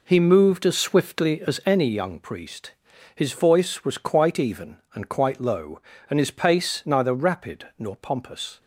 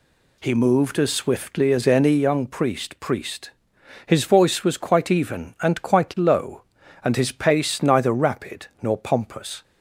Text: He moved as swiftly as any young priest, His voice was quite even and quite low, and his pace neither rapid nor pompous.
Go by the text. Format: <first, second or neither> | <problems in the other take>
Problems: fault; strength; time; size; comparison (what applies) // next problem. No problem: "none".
first | says "priest" twice; at 3.0 s // pauses between "rapid" and "nor"; slight; at 8.6 s; 0.16 s long